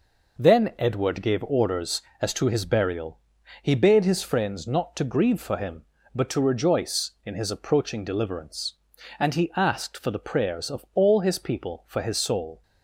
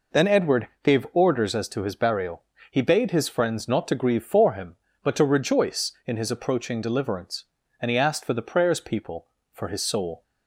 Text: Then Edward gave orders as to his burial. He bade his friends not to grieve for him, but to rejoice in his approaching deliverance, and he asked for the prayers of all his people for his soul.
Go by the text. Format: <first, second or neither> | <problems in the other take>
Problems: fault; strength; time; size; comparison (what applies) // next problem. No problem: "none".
first | pauses between "Edward" and "gave"; slight; at 0.6 s; 0.16 s long // skips "of all his"; at 8.8 s